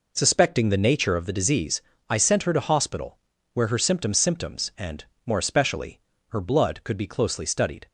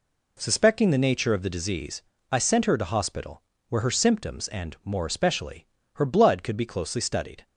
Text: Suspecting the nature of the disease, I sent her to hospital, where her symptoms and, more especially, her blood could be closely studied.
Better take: second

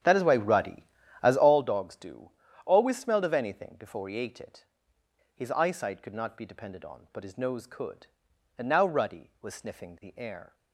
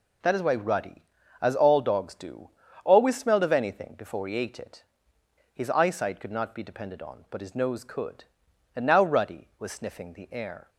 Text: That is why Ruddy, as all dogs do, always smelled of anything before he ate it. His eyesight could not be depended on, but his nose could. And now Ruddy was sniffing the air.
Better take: second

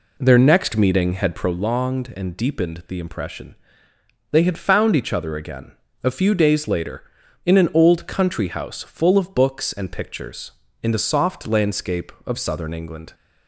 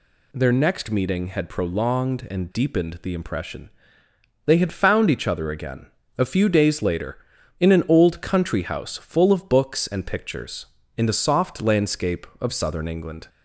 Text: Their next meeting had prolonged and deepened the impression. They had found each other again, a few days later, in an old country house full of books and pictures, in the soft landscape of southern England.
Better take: second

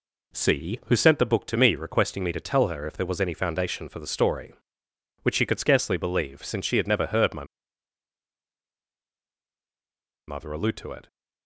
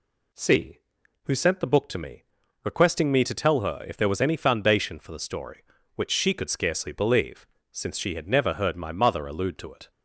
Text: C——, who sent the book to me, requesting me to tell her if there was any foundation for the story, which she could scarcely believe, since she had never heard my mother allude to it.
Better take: second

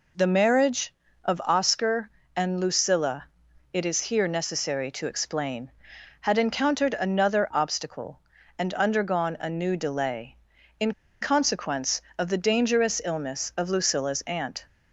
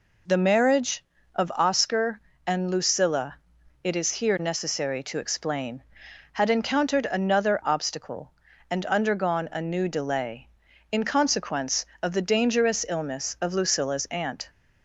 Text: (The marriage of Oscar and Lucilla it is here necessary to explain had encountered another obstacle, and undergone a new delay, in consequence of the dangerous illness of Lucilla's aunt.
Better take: second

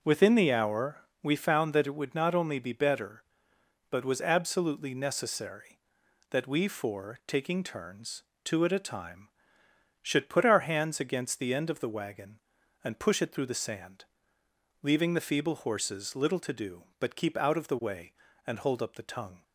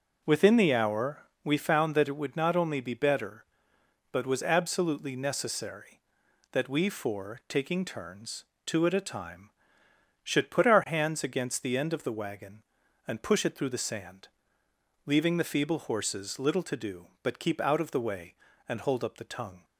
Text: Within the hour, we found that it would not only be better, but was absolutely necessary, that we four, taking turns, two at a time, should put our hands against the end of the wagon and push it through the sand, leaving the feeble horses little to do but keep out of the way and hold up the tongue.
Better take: neither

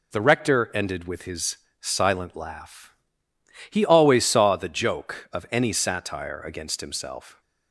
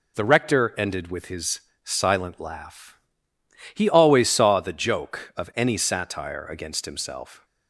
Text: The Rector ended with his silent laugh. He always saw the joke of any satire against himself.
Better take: neither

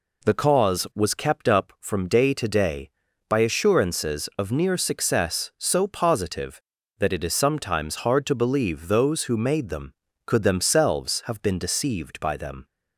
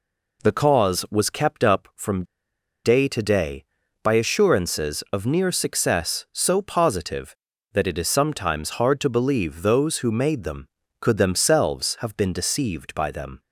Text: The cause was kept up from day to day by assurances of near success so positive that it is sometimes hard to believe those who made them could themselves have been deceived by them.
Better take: first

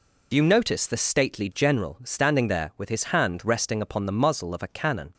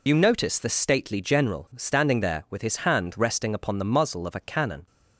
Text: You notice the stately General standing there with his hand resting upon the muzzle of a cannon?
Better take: first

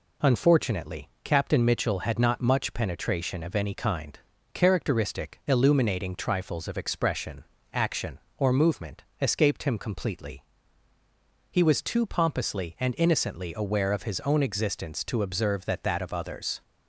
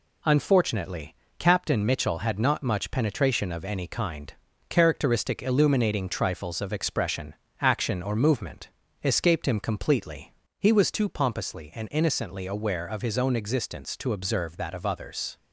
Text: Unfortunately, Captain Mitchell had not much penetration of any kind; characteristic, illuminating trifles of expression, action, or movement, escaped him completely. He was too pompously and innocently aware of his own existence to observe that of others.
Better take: second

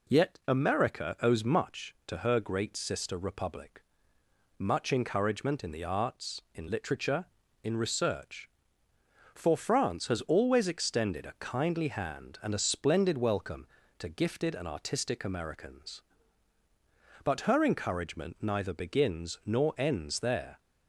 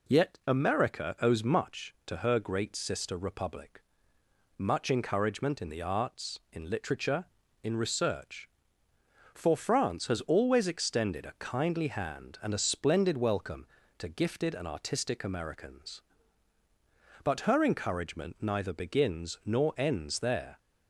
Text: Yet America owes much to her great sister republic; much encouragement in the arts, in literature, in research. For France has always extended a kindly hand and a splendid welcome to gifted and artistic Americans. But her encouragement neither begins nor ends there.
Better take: neither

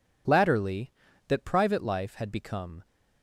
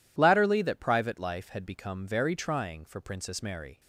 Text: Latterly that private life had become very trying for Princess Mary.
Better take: second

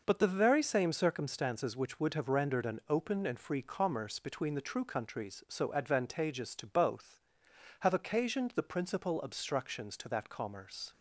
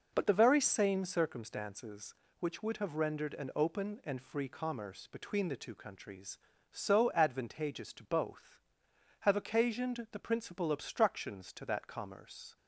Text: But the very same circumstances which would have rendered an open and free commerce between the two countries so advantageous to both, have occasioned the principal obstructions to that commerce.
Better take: second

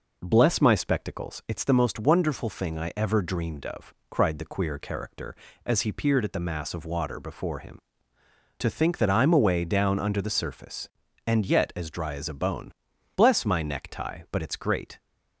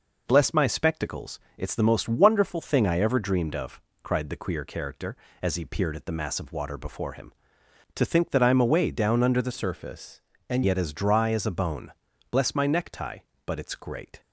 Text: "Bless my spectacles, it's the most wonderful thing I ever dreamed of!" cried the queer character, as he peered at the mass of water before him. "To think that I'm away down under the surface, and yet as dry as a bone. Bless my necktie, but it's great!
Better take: first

